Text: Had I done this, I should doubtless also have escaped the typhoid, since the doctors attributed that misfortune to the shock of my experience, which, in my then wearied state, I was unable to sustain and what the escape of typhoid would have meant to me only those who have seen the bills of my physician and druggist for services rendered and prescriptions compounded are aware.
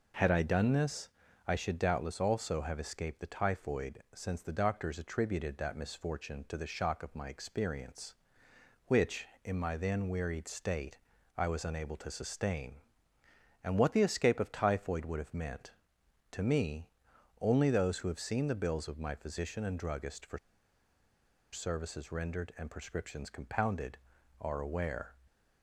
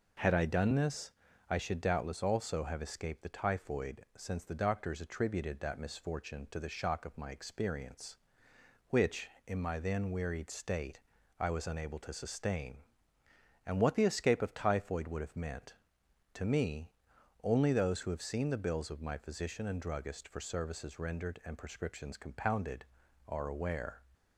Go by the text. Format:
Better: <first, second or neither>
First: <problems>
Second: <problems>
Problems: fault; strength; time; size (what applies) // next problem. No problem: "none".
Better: second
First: pauses between "me" and "only"; noticeable; at 16.8 s; 0.56 s long // pauses between "for" and "services"; at 20.3 s; 1.1 s long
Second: pauses between "me" and "only"; noticeable; at 16.8 s; 0.56 s long